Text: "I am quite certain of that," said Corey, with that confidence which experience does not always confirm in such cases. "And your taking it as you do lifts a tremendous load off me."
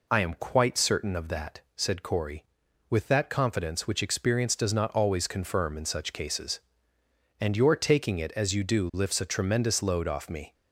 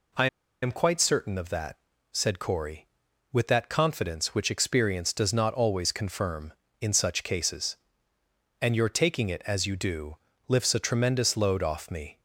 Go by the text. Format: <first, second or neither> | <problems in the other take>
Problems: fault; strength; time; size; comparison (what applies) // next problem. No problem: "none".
first | pauses between "I" and "am"; slight; at 0.2 s; 0.35 s long // pauses between "do" and "lifts"; slight; at 10.1 s; 0.30 s long